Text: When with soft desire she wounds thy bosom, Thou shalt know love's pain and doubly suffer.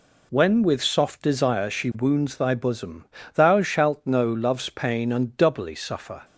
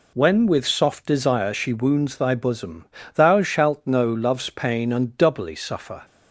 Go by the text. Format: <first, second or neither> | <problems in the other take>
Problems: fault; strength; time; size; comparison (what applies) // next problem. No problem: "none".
neither | none